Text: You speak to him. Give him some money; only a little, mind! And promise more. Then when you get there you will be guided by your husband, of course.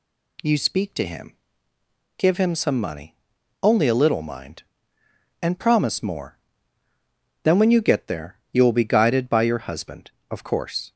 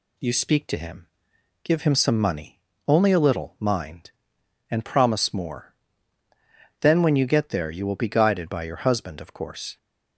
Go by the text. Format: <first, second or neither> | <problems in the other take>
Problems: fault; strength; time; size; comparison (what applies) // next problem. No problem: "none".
neither | none